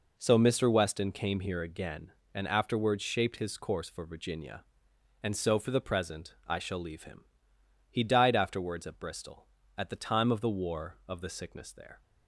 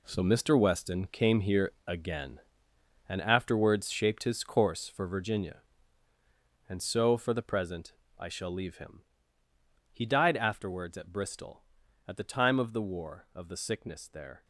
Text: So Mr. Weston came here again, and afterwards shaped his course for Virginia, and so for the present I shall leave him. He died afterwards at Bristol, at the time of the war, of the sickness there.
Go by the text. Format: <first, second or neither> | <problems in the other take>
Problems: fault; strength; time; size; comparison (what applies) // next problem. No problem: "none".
first | gets quieter; strong; throughout; 11.5 dB // pauses between "here" and "again"; slight; at 1.7 s; 0.16 s long // pauses between "present" and "I"; slight; at 7.9 s; 0.26 s long